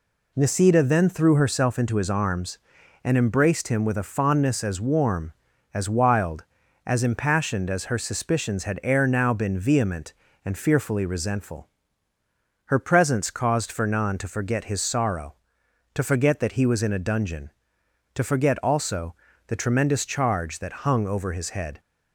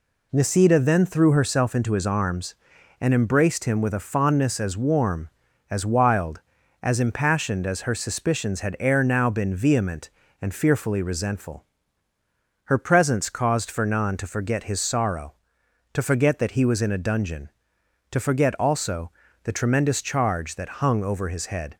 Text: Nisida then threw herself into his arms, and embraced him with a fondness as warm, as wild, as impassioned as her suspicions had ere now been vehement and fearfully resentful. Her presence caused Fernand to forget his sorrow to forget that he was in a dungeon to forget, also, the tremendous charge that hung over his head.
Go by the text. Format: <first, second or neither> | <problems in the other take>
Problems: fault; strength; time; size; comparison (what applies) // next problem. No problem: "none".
neither | none